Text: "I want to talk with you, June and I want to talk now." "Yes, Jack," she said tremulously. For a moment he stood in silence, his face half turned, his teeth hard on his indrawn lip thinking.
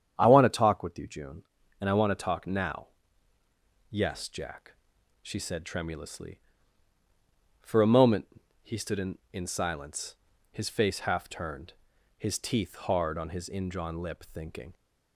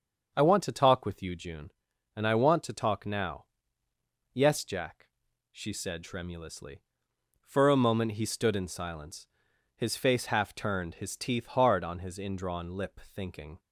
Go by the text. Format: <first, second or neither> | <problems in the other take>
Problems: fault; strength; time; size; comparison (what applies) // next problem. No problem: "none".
second | starts louder than the rest; strong; until 1.1 s; 8.5 dB; also in the second // pauses between "moment" and "he"; at 8.2 s; 0.38 s long // says "in" twice; at 9.3 s